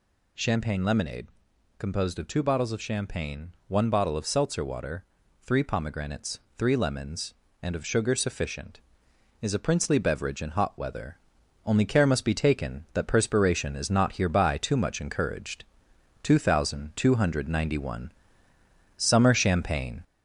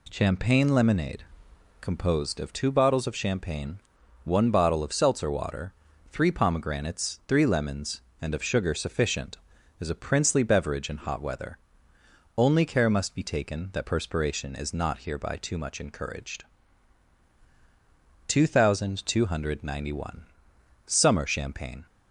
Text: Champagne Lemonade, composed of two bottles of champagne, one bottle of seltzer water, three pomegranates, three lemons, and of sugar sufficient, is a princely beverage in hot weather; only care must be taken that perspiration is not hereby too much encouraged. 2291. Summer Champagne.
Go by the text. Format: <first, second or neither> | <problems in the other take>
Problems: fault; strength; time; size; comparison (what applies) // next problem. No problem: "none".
second | gets louder; slight; throughout; 3 dB